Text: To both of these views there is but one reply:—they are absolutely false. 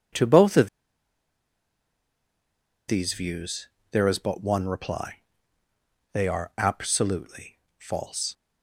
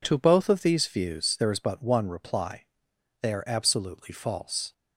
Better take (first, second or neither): second